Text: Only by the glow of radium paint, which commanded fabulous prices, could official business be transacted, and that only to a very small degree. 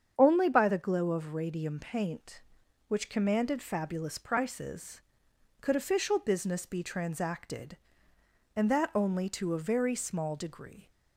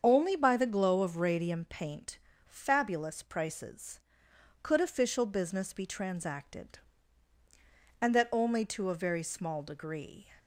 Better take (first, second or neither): first